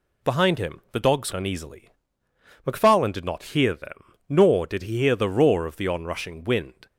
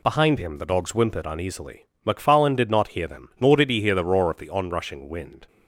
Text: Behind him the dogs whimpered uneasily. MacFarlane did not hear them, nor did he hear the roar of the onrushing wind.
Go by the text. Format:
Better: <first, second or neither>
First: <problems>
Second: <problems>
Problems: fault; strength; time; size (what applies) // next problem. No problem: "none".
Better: second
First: skips "whimpered"; at 1.3 s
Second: none